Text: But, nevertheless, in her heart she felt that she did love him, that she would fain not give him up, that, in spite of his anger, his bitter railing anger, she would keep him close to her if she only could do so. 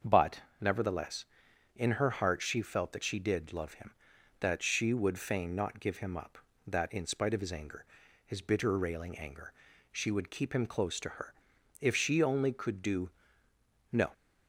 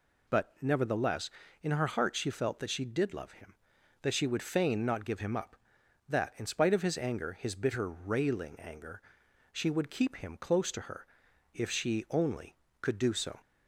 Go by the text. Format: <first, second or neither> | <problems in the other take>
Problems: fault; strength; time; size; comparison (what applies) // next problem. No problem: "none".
second | starts louder than the rest; until 1.2 s; 6.5 dB // pauses between "her" and "if"; noticeable; at 11.3 s; 0.48 s long; noticeable in the second // says "no" for "so"; at 13.9 s